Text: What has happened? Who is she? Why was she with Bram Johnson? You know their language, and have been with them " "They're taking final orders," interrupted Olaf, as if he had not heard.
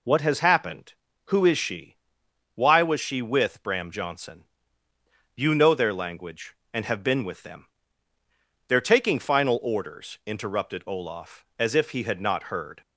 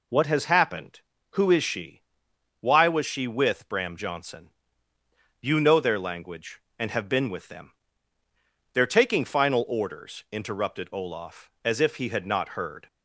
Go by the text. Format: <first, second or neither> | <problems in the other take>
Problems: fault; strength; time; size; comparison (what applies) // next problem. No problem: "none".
neither | none